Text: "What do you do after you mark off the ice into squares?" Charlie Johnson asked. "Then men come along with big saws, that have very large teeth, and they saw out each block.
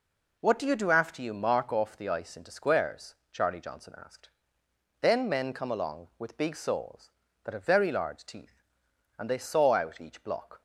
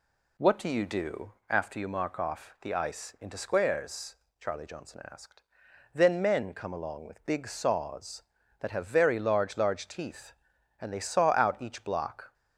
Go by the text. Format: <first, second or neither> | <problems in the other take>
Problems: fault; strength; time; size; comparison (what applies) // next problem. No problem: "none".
first | says "large" twice; at 9.5 s